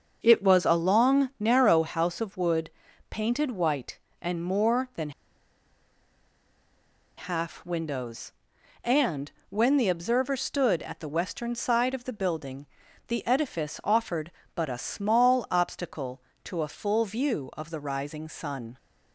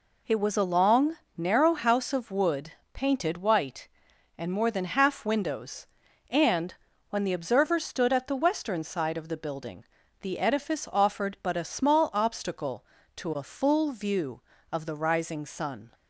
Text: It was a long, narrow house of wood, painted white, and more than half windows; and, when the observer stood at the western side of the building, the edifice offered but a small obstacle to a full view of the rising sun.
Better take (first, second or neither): second